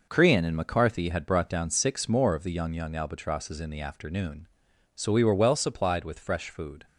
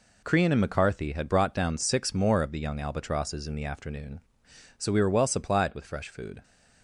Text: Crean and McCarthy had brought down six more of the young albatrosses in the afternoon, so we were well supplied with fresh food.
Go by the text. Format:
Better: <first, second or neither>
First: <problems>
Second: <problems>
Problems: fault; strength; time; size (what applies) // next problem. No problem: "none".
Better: second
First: says "young" twice; at 2.7 s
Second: none